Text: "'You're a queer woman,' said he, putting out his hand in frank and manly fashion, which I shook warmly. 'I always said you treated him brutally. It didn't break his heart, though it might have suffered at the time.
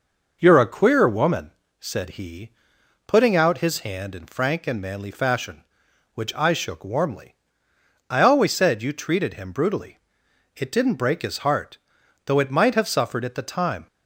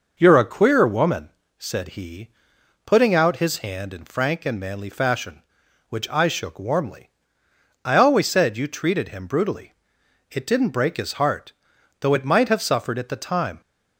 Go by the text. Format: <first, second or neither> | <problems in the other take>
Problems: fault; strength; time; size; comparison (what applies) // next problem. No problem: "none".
neither | none